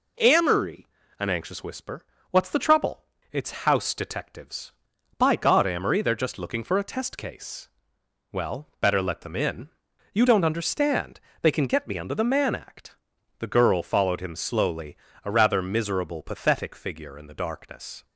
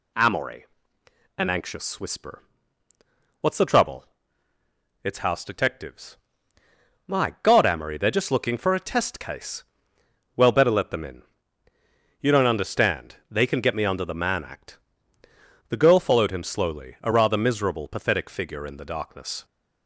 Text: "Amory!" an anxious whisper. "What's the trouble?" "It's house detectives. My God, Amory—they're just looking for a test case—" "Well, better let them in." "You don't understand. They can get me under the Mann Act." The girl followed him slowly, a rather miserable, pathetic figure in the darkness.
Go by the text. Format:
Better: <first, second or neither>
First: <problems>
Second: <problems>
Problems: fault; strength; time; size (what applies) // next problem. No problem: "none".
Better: second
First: says "By" for "My"; at 5.1 s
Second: none